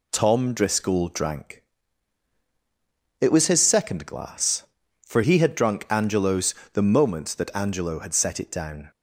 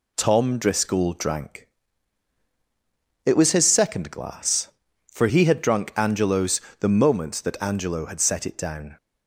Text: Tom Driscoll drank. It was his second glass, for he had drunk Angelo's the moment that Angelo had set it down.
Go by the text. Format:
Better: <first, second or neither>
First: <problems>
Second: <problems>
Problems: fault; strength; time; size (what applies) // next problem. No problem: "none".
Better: neither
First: pauses between "Angelo's" and "the"; slight; at 6.5 s; 0.18 s long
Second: pauses between "Angelo's" and "the"; slight; at 6.6 s; 0.18 s long